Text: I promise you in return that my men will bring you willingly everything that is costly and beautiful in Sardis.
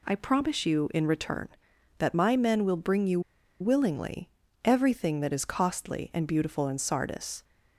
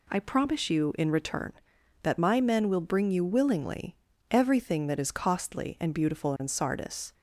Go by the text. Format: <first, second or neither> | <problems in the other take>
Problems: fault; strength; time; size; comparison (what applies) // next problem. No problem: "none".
second | pauses between "you" and "willingly"; at 3.1 s; 0.40 s long // pauses between "willingly" and "everything"; slight; at 4.2 s; 0.34 s long; slight in the second